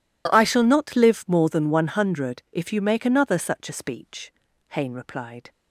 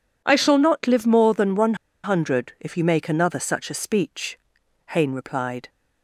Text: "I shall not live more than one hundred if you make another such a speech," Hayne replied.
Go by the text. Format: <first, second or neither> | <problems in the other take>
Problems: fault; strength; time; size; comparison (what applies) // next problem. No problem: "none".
first | pauses between "one" and "hundred"; slight; at 1.7 s; 0.29 s long